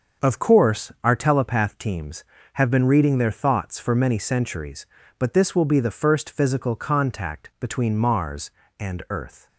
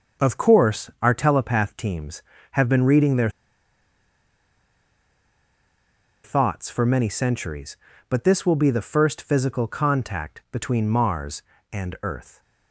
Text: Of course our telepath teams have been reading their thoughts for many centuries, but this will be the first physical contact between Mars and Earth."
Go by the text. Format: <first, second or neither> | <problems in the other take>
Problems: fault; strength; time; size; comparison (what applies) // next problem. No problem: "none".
first | starts louder than the rest; until 1.3 s; 6.5 dB; also in the first // pauses between "their" and "thoughts"; strong; at 3.2 s; 2.9 s long